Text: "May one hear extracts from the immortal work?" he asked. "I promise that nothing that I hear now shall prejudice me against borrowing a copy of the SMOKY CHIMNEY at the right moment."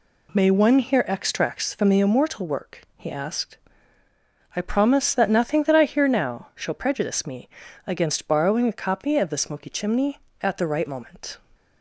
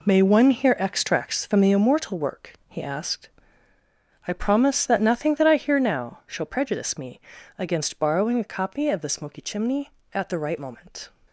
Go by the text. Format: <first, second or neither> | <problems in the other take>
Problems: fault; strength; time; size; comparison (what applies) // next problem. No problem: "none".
first | gets quieter; strong; throughout; 10.5 dB // pauses between "me" and "against"; slight; at 7.1 s; 0.36 s long; slight in the first